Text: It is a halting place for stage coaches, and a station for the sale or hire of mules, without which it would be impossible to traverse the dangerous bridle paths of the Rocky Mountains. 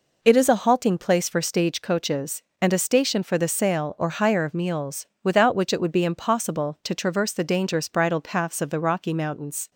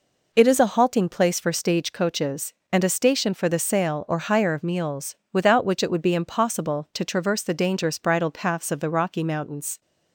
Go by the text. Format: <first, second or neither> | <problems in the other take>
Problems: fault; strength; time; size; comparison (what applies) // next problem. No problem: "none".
neither | none